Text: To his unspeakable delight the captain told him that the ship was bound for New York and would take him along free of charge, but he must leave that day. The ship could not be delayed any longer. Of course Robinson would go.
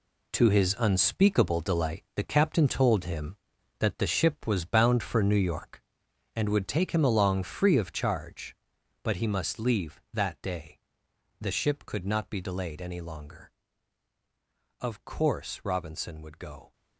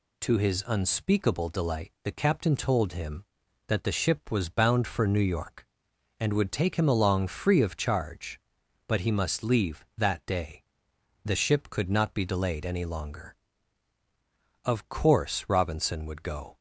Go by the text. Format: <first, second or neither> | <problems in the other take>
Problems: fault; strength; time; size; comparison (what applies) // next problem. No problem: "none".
second | gets quieter; strong; throughout; 10 dB